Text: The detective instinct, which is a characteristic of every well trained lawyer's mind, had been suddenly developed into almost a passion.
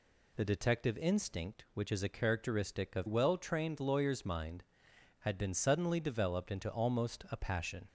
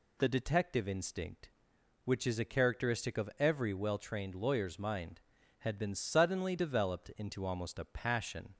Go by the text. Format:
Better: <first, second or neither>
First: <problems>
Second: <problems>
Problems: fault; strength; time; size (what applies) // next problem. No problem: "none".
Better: second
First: skips "every"; at 3.0 s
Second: none